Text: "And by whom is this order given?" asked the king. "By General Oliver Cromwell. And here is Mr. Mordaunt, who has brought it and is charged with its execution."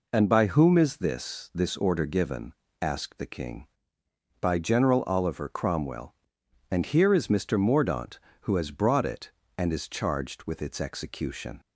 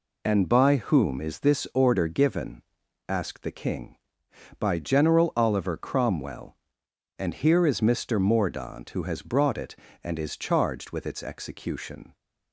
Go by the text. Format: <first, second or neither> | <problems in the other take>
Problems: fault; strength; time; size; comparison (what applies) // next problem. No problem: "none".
second | says "this" twice; at 1.5 s